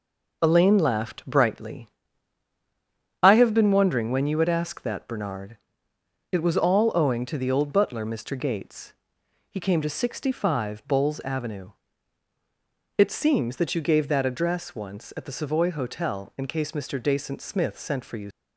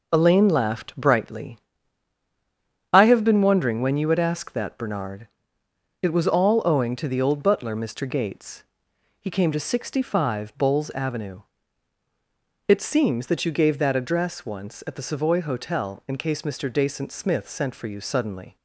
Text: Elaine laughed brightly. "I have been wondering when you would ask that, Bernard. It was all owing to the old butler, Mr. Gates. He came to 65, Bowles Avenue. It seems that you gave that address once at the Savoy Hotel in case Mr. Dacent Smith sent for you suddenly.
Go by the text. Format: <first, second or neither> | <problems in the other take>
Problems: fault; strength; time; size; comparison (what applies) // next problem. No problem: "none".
second | stops before "suddenly"; at 18.3 s